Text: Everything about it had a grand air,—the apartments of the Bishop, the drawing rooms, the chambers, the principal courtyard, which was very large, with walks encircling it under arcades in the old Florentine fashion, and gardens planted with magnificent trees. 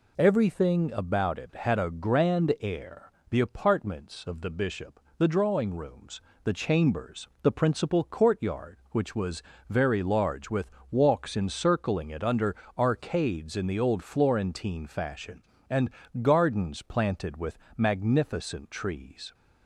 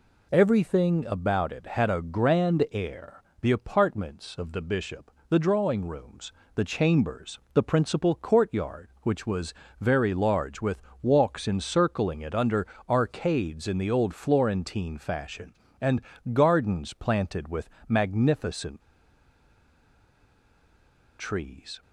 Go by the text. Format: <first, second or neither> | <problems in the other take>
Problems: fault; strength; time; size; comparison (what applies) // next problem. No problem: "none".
first | pauses between "was" and "very"; slight; at 9.5 s; 0.26 s long; slight in the first // pauses between "with" and "walks"; slight; at 10.8 s; 0.18 s long; slight in the first // pauses between "under" and "arcades"; slight; at 12.6 s; 0.20 s long; slight in the first // pauses between "and" and "gardens"; slight; at 15.9 s; 0.32 s long; slight in the first // pauses between "with" and "magnificent"; slight; at 17.6 s; 0.22 s long; slight in the first // pauses between "magnificent" and "trees"; strong; at 18.8 s; 2.3 s long